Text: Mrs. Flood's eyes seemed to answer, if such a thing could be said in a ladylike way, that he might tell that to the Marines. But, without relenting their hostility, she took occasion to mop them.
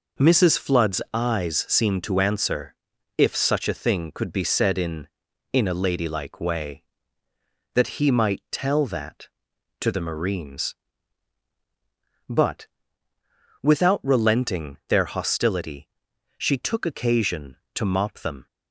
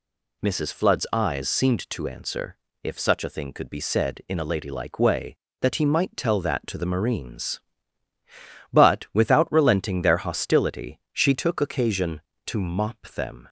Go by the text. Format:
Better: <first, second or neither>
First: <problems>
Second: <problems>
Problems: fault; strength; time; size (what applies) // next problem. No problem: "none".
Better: second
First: says "in" twice; at 5.5 s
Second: none